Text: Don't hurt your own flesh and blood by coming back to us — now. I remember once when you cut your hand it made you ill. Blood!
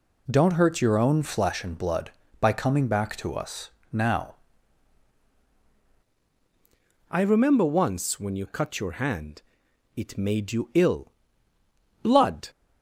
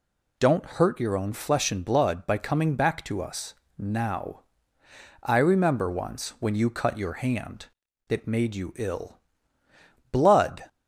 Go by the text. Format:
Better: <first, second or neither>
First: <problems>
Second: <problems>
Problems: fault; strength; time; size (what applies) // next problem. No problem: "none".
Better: second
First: changes voice at "I"; from 7.0 s on; 5.4 s long // pauses between "hand" and "it"; noticeable; at 9.4 s; 0.54 s long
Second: pauses between "hand" and "it"; at 7.6 s; 0.42 s long